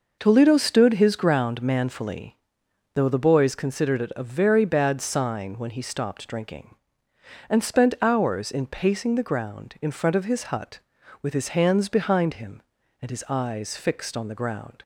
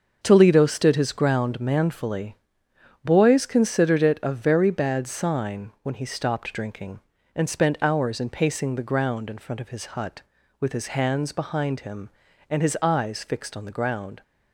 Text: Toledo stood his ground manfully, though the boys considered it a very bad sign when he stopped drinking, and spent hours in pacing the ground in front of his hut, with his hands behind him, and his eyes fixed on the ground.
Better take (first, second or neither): first